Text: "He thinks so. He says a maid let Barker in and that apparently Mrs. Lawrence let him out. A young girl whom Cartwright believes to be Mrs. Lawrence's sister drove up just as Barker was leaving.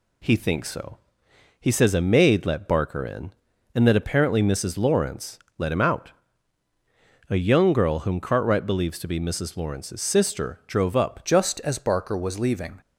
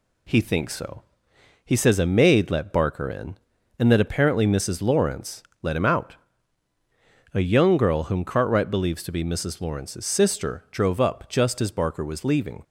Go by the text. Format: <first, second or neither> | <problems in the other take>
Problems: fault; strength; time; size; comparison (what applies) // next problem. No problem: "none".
second | pauses between "Lawrence" and "let"; slight; at 5.3 s; 0.20 s long; slight in the second // changes voice at "just"; from 11.2 s on; 1.6 s long